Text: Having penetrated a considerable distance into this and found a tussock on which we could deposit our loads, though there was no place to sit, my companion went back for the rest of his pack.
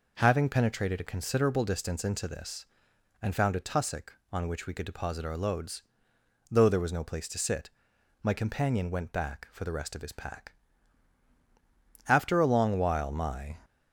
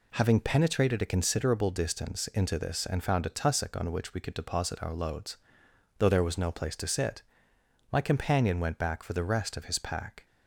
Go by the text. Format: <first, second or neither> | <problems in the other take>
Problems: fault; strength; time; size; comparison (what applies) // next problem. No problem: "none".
second | goes on to say "After a long while my"; from 12.0 s on; 1.5 s long